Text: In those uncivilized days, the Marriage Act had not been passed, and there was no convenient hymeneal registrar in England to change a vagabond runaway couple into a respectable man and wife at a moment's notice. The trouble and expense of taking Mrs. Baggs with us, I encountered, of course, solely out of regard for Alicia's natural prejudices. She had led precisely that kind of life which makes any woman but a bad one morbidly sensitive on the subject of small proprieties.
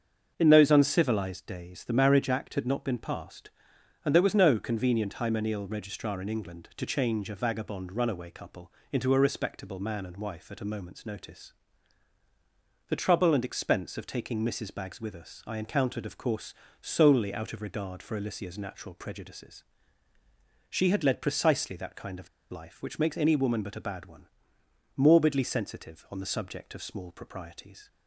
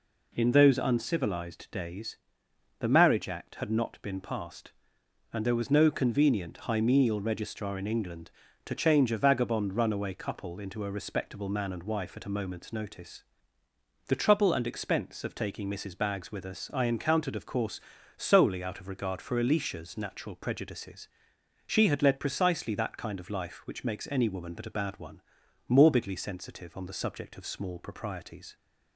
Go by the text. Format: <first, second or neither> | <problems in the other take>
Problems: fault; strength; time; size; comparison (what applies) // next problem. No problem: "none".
second | starts louder than the rest; until 1.3 s; 7 dB // pauses between "couple" and "into"; slight; at 8.7 s; 0.18 s long // pauses between "of" and "life"; slight; at 22.2 s; 0.22 s long // pauses between "one" and "morbidly"; noticeable; at 24.2 s; 0.72 s long; also in the second